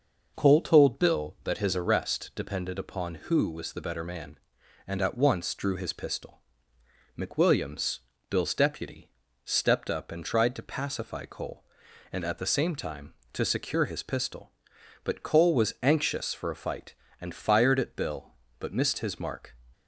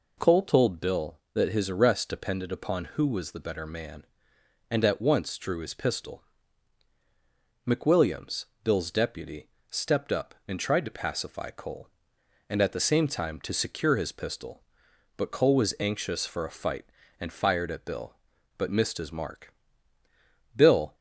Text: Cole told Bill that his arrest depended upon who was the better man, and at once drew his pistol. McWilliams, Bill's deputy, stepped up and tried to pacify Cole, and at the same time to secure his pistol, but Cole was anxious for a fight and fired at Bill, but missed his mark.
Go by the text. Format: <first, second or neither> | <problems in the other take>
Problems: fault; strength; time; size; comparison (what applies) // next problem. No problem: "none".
first | goes on to say "Bill"; slight; from 20.5 s on; 0.38 s long